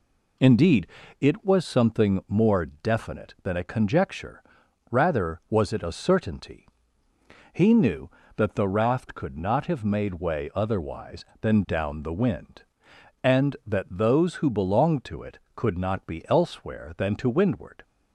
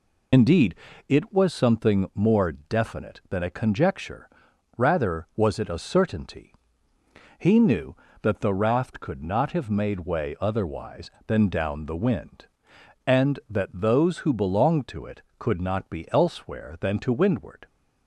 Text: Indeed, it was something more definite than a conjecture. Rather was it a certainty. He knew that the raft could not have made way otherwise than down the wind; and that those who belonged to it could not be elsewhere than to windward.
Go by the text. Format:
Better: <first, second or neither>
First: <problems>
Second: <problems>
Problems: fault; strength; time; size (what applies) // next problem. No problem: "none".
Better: first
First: none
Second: loses the start of "Indeed"; at 0.3 s; 50 ms